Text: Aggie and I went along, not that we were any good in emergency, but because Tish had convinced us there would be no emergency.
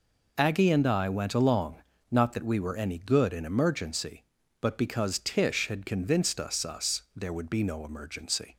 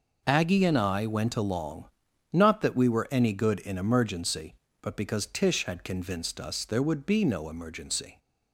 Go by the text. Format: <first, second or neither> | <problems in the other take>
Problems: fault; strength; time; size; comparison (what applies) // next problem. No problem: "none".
second | says "us" twice; at 6.6 s